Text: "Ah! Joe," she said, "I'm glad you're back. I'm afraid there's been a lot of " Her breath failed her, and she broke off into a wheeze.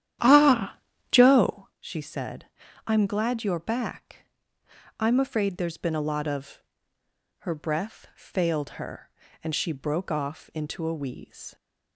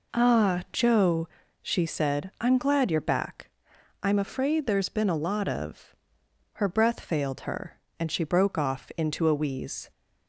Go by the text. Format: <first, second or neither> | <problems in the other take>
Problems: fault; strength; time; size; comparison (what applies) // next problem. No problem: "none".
second | starts louder than the rest; strong; until 1.8 s; 11.5 dB